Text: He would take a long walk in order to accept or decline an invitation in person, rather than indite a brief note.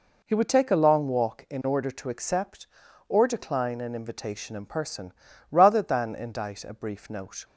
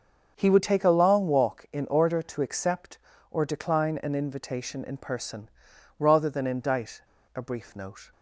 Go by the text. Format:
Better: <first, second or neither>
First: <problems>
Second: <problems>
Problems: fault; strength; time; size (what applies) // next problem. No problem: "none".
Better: first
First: none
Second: starts louder than the rest; until 1.3 s; 6.5 dB // pauses between "indite" and "a"; slight; at 7.0 s; 0.34 s long